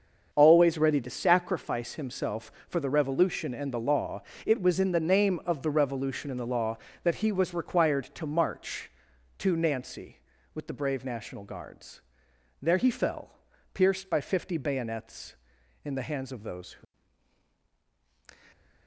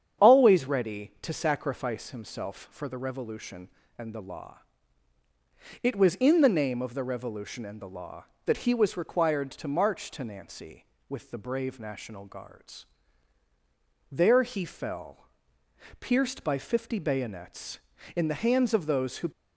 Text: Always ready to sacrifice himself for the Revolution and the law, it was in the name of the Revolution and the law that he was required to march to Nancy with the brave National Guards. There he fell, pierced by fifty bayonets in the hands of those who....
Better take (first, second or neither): second